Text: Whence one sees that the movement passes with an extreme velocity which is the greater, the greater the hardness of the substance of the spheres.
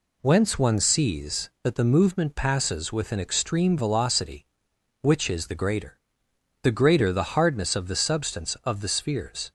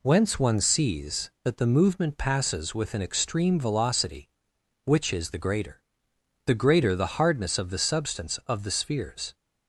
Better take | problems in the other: neither | none

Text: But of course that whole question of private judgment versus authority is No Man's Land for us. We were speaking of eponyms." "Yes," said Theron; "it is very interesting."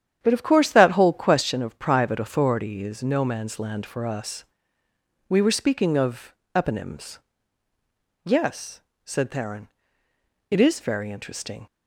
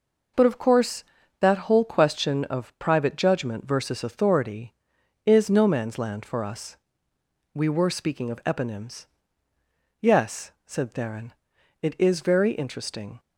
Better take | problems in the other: second | starts louder than the rest; strong; until 1.2 s; 9.5 dB // skips "judgment versus"; at 2.1 s // pauses between "of" and "eponyms"; slight; at 6.3 s; 0.22 s long

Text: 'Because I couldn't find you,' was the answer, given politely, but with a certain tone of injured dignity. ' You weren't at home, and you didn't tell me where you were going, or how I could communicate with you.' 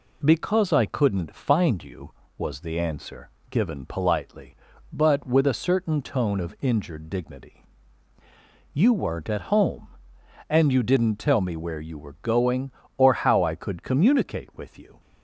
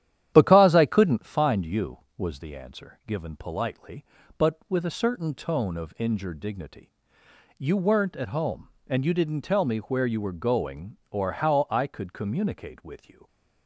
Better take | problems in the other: first | starts louder than the rest; strong; until 1.3 s; 11 dB

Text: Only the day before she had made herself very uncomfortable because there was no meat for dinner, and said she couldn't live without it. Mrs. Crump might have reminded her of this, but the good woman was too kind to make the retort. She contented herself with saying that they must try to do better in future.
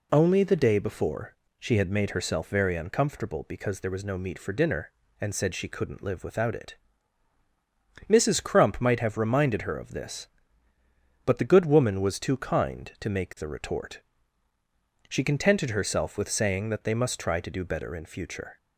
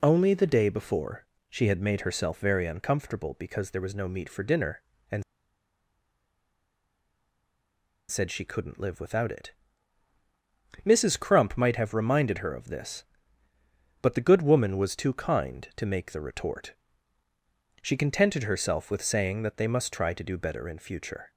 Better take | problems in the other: first | pauses between "before" and "she"; slight; at 1.2 s; 0.24 s long; slight in the first // pauses between "and" and "said"; strong; at 5.2 s; 2.8 s long

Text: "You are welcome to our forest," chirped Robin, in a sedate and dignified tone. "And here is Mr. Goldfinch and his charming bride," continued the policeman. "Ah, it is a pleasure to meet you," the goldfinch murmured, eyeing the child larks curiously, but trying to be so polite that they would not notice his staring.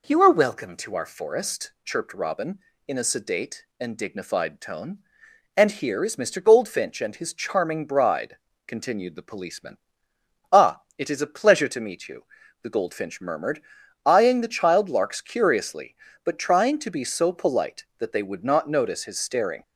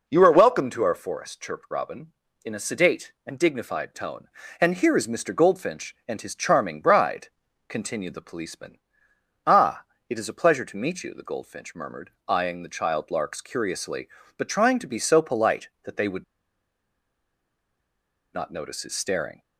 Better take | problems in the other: first | pauses between "would" and "not"; strong; at 16.2 s; 2.0 s long

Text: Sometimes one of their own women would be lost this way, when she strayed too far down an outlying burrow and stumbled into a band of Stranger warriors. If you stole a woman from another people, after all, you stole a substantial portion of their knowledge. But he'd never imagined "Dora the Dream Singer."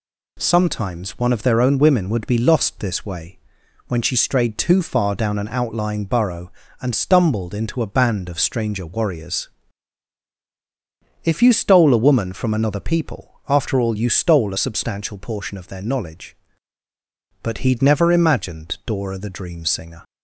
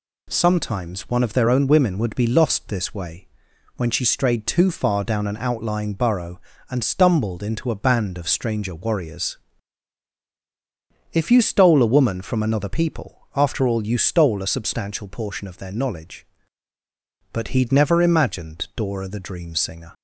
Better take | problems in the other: neither | none

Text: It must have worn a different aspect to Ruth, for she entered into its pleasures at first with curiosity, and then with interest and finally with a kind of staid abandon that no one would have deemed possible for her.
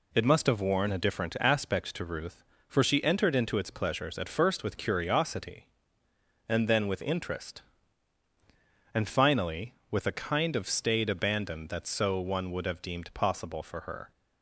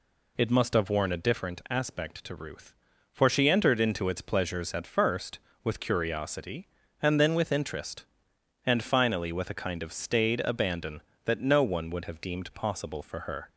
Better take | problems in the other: second | says "so" for "no"; at 11.8 s

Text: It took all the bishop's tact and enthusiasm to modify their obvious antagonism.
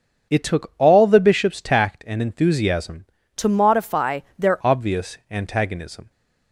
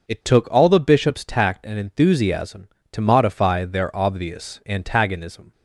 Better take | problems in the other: second | starts louder than the rest; until 1.3 s; 7 dB // changes voice from "to" to "their"; from 3.3 to 4.5 s; 1.2 s long // pauses between "modify" and "their"; slight; at 4.2 s; 0.18 s long

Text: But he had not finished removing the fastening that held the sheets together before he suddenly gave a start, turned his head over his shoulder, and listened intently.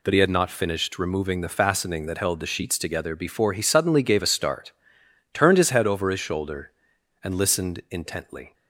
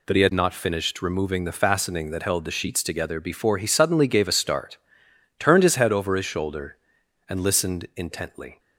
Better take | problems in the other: neither | none

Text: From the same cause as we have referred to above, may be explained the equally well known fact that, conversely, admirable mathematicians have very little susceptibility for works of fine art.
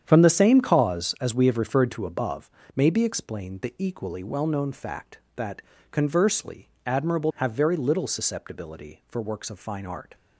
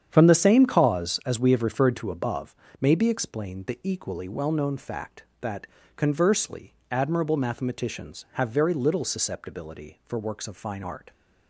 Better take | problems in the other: second | starts louder than the rest; strong; until 1.0 s; 8.5 dB; strong in the second // skips "mathematicians"; at 7.3 s

